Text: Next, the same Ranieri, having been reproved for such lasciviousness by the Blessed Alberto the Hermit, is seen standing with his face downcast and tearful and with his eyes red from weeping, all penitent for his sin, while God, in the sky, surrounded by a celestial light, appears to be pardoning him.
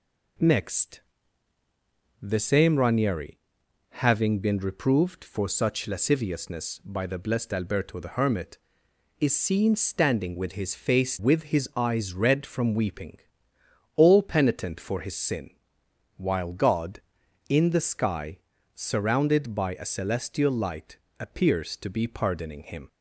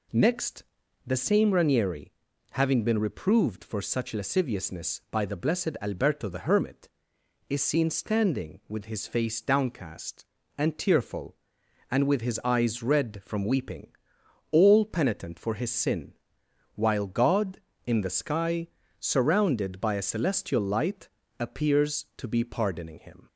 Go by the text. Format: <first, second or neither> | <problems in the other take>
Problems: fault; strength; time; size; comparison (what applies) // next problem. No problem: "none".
second | skips "downcast and tearful and"; at 11.1 s